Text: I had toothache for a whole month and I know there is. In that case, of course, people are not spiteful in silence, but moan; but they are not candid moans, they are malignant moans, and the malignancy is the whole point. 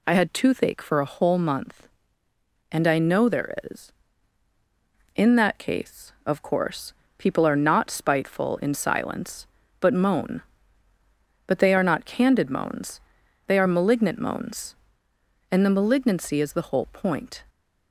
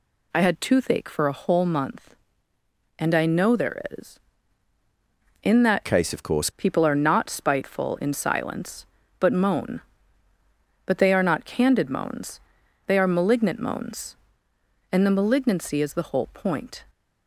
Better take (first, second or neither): first